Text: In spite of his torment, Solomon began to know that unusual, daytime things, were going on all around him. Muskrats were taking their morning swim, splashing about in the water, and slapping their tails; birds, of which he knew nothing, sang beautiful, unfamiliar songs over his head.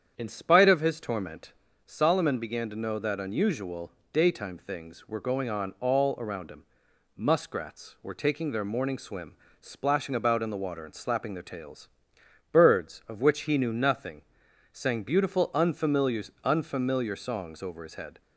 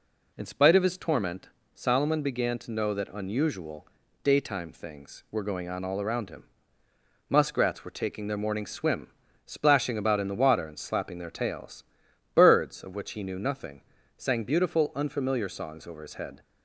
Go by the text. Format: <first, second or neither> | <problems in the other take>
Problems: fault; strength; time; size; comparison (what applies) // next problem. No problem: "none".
second | starts louder than the rest; strong; until 1.1 s; 8.5 dB // says "unfamiliar" twice; at 16.4 s